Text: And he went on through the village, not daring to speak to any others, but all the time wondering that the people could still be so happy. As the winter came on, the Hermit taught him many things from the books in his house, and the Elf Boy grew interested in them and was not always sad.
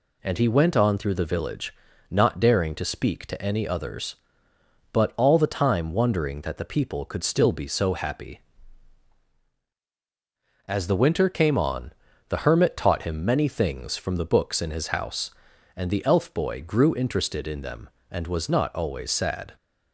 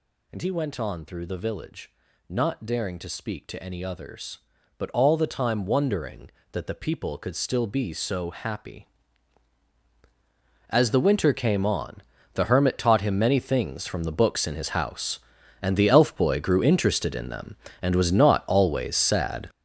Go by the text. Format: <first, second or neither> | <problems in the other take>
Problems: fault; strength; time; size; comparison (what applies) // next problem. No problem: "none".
first | gets louder; strong; throughout; 11 dB